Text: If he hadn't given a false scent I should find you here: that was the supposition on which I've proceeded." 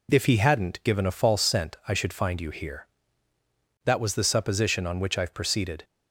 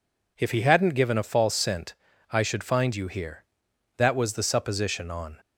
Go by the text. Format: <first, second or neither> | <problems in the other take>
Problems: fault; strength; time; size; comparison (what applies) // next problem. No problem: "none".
first | pauses between "scent" and "I"; at 1.9 s; 0.38 s long // stops before "which I've proceeded"; at 5.3 s